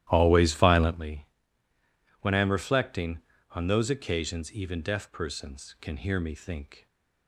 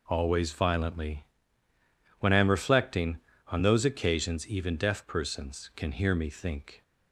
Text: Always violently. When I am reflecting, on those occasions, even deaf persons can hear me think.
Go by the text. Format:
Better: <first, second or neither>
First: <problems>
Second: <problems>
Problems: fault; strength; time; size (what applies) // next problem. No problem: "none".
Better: second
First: starts louder than the rest; strong; until 1.0 s; 14 dB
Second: none